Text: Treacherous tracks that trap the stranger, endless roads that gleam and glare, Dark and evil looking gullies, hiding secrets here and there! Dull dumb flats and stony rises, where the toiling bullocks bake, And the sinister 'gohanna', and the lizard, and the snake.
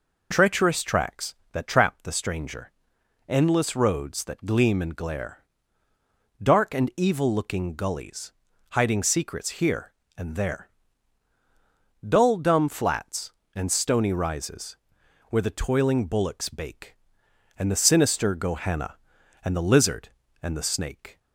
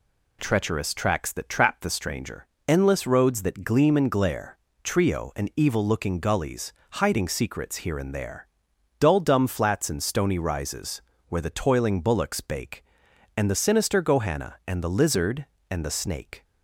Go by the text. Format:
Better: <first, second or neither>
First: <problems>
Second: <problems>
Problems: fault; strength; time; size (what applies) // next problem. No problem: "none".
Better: first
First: none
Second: says "Trio" for "Dark"; at 4.8 s